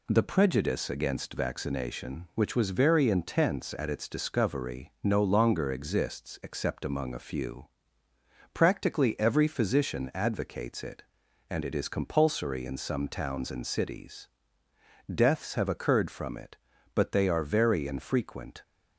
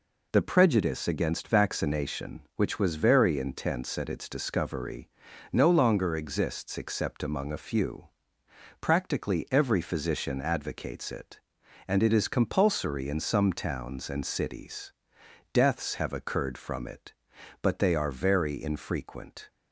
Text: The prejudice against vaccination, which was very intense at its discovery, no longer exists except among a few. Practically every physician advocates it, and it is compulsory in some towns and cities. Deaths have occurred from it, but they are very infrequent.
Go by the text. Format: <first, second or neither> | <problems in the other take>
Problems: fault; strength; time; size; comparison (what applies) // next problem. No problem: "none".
neither | none